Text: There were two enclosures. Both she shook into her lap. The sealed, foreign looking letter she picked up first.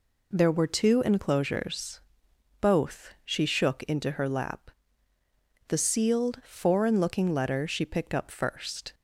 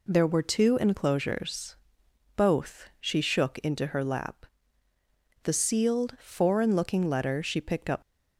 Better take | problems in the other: first | stops before "first"; at 8.0 s

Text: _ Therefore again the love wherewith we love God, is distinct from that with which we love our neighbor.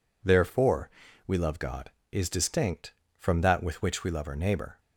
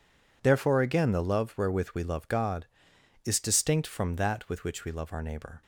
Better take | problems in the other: second | skips "again the love wherewith"; at 1.0 s

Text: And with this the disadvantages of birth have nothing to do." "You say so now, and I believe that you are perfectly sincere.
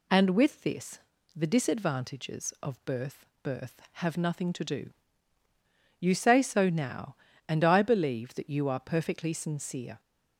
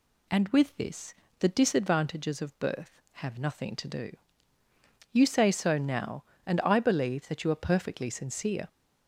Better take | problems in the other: second | pauses between "this" and "the"; slight; at 0.9 s; 0.36 s long; slight in the second // says "birth" twice; at 3.4 s

